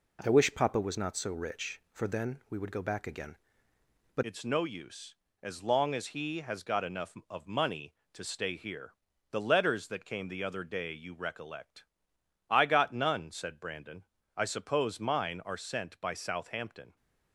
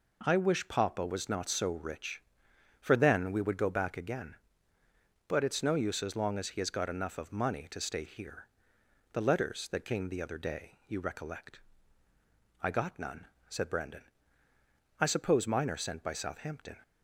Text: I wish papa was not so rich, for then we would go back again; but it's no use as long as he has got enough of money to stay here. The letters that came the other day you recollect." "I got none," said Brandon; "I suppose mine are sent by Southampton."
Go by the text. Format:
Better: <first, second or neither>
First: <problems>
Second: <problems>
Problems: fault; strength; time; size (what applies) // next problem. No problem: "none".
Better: second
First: changes voice at "it's"; from 4.2 s on; 12.7 s long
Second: none